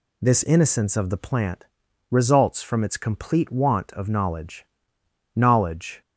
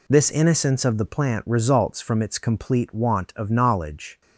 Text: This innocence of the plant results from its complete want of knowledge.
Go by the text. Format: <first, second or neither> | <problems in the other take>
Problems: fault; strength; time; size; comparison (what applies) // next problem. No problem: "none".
second | pauses between "plant" and "results"; noticeable; at 1.6 s; 0.48 s long // says "knowledge" twice; at 5.3 s